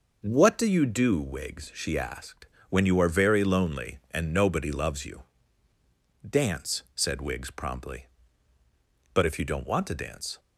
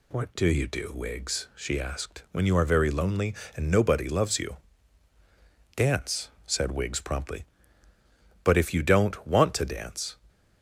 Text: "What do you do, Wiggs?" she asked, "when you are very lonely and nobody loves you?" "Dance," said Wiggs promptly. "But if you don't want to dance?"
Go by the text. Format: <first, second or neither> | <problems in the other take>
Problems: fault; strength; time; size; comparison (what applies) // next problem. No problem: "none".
neither | none